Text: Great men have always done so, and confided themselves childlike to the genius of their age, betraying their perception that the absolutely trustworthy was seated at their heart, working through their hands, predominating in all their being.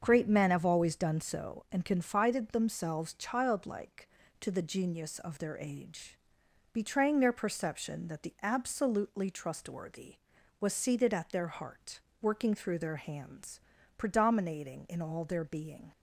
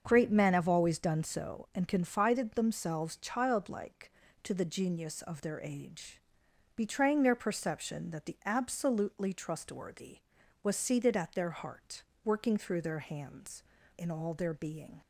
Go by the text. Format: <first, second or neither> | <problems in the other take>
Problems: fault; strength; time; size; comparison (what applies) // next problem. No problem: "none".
first | starts louder than the rest; until 1.0 s; 7 dB; also in the first // skips "predominating"; at 13.8 s